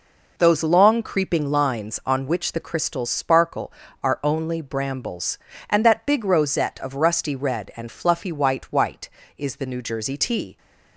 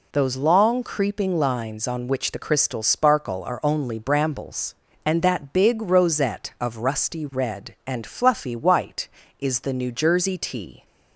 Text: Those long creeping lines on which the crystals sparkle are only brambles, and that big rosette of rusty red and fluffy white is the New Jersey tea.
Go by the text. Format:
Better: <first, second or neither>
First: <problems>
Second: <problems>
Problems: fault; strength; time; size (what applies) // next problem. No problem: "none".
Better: second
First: says "white" twice; at 8.7 s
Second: none